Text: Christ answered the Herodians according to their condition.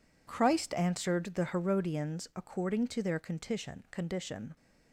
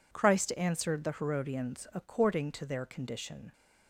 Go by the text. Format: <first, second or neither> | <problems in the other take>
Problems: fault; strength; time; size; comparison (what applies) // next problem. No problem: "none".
second | says "condition" twice; at 3.9 s